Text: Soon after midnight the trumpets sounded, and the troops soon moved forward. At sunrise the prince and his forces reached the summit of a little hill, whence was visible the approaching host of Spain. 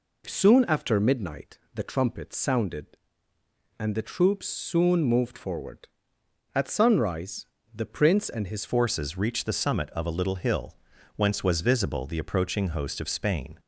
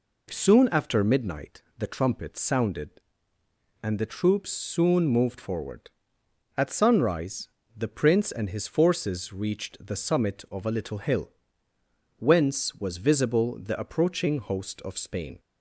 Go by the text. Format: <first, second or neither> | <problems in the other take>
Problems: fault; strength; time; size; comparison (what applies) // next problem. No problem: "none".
second | pauses between "midnight" and "the"; slight; at 1.5 s; 0.16 s long; slight in the second // pauses between "sunrise" and "the"; slight; at 7.4 s; 0.30 s long; slight in the second // changes voice at "forces"; from 8.6 s on; 4.9 s long